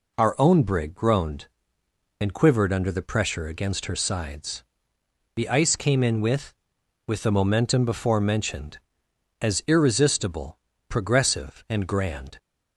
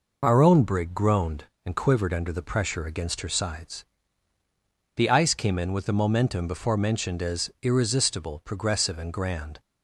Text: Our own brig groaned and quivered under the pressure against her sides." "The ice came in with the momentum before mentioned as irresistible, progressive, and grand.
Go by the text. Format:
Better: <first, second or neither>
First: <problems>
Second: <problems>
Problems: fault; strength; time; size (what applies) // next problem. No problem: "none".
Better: second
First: says "with" twice; at 7.0 s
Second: none